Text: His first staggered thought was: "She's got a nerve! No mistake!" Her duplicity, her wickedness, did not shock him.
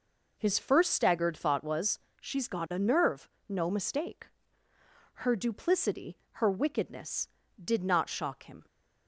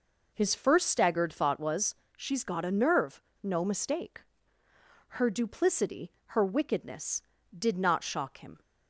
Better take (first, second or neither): neither